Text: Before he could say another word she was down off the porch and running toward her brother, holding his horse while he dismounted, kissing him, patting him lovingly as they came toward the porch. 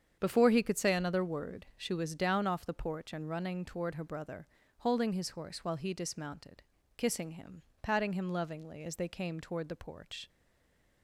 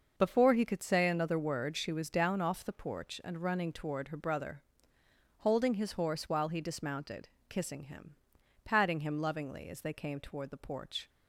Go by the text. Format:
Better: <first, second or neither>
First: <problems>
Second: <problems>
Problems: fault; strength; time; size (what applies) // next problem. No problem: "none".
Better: second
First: starts louder than the rest; strong; until 1.2 s; 8 dB // stays silent after the last word; slight; from 10.2 s on; 0.8 s long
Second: starts louder than the rest; noticeable; until 1.1 s; 6 dB